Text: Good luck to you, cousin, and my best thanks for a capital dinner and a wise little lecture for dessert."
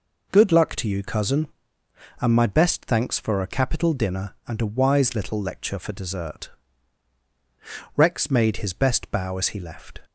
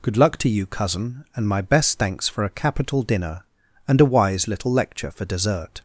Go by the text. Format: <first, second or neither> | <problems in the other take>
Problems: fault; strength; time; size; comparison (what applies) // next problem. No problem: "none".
second | goes on to say "Rex made his best bow as he left"; strong; from 7.9 s on; 2.0 s long